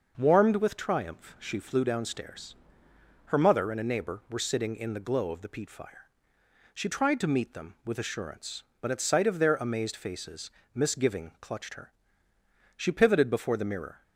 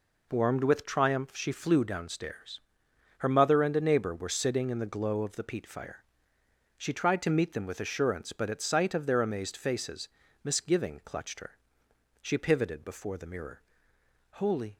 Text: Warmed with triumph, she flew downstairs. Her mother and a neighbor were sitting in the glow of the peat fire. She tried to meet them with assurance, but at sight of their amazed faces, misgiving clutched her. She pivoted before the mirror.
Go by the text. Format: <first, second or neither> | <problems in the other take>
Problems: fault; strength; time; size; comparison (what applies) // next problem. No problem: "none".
first | goes on to say "Holy"; slight; from 14.3 s on; 0.44 s long